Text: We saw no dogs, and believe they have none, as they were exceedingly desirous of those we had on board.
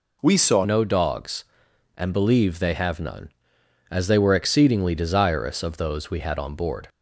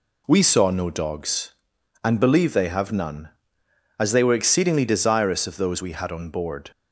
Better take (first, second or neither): second